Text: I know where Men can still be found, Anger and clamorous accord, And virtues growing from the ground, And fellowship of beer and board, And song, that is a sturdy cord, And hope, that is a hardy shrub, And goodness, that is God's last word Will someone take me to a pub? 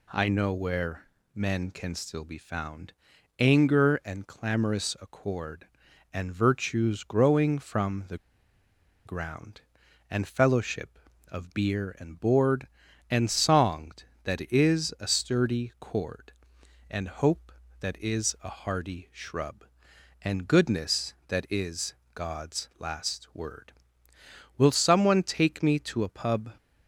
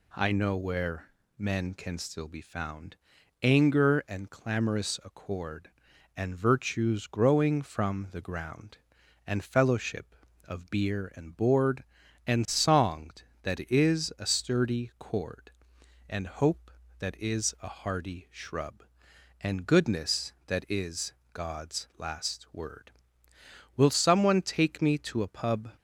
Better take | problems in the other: second | pauses between "where" and "Men"; slight; at 1.0 s; 0.30 s long; slight in the second // pauses between "the" and "ground"; noticeable; at 8.1 s; 0.88 s long // pauses between "is" and "God's"; slight; at 21.9 s; 0.20 s long; slight in the second

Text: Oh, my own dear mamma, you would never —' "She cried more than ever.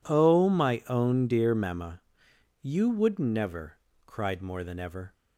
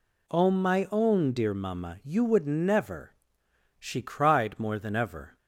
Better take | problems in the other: second | skips "She"; at 3.9 s

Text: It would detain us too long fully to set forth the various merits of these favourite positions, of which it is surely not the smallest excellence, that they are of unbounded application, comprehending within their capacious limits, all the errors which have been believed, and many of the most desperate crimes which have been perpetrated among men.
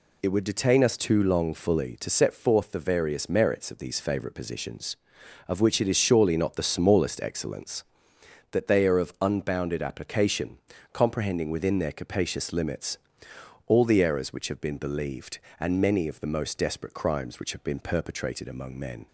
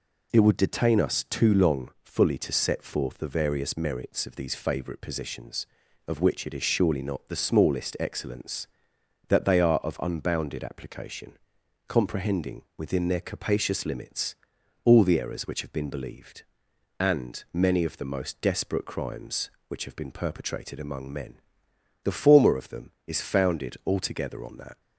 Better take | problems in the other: first | goes on to say "The former of them is founded altogether on that"; strong; from 22.0 s on; 2.7 s long

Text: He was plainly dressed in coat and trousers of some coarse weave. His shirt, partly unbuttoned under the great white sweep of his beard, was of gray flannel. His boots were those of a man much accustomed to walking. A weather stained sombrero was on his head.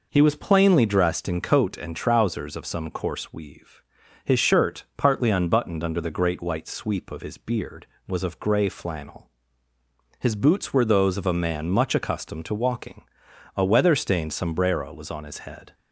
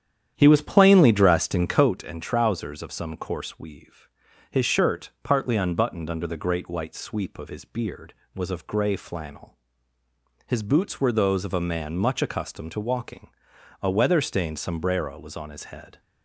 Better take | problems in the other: first | starts louder than the rest; strong; until 1.9 s; 9.5 dB

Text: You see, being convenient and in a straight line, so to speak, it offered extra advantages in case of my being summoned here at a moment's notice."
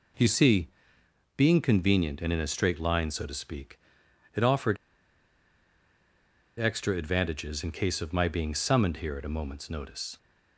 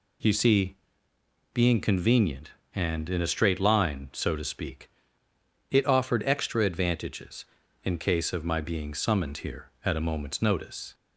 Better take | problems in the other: second | pauses between "offered" and "extra"; strong; at 4.7 s; 1.8 s long

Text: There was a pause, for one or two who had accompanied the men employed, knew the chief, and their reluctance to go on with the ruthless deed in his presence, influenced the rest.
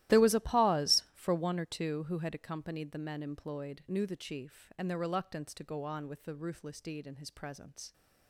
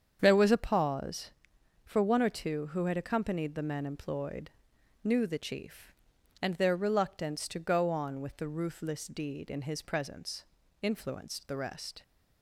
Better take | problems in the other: second | starts louder than the rest; strong; until 1.2 s; 15 dB; strong in the second // stops before "influenced the rest"; at 7.9 s

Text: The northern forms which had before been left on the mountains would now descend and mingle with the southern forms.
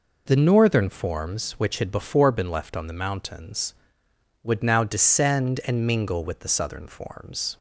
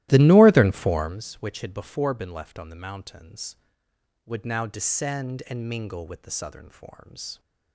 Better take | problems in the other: first | starts louder than the rest; strong; until 1.2 s; 15.5 dB

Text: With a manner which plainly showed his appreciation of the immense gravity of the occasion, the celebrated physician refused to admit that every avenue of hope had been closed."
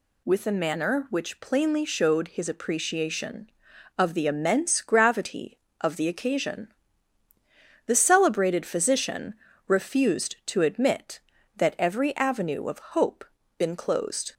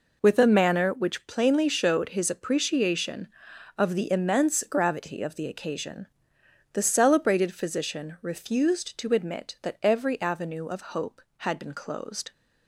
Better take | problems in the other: second | pauses between "physician" and "refused"; slight; at 9.3 s; 0.34 s long // skips "had"; at 13.4 s

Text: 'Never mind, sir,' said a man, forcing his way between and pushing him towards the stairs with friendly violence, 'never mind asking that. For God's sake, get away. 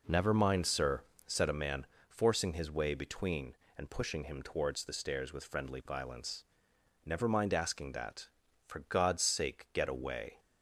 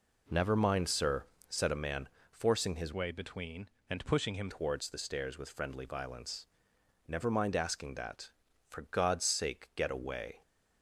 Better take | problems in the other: first | changes voice from "way" to "him"; from 2.9 to 4.5 s; 1.6 s long

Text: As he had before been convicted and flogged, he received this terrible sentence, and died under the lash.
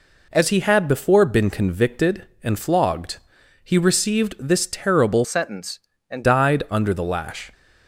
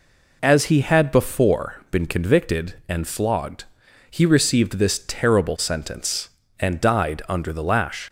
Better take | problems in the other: second | changes voice from "sentence" to "and"; from 5.2 to 6.2 s; 1.0 s long

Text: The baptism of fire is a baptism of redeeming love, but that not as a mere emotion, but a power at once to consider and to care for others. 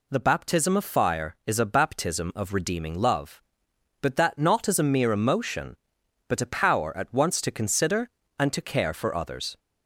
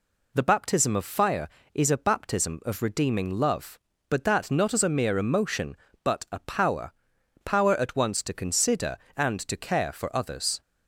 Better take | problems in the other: first | says "power" twice; at 7.4 s

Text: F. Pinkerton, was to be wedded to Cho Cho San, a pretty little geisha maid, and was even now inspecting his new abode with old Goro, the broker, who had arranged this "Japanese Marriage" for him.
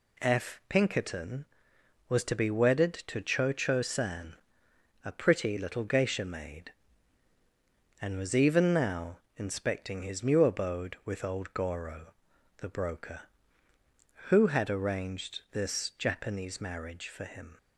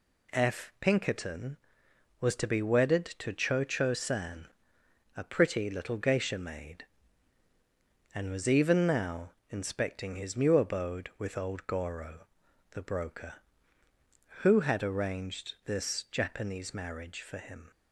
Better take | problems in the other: neither | pauses between "now" and "inspecting"; slight; the same in both

